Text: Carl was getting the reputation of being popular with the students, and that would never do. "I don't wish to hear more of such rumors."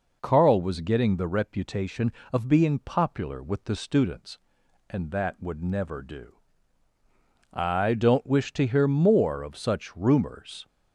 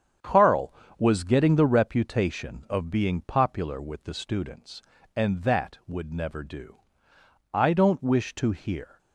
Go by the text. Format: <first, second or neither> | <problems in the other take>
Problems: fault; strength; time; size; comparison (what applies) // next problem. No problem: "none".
first | starts louder than the rest; strong; until 1.4 s; 8 dB // stops before "more of such rumors"; at 8.9 s